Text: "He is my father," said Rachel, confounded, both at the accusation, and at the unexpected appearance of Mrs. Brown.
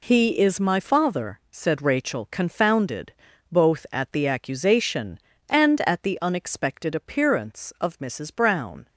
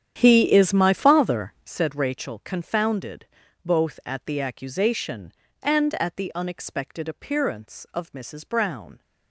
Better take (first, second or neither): first